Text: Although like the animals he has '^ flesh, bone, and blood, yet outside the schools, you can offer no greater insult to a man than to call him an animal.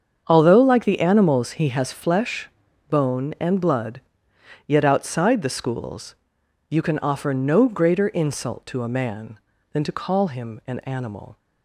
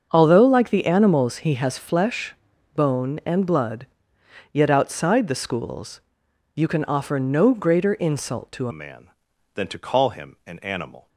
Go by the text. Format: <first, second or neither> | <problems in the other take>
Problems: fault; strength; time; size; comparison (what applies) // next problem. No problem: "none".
first | starts louder than the rest; until 1.1 s; 7 dB; strong in the first // changes voice at "a"; from 8.7 s on; 2.3 s long